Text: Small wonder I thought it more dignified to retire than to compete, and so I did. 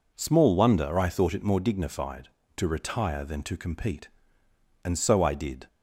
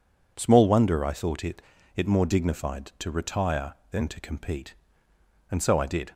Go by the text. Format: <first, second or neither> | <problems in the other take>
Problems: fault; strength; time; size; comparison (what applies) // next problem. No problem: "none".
first | says "it" twice; at 1.9 s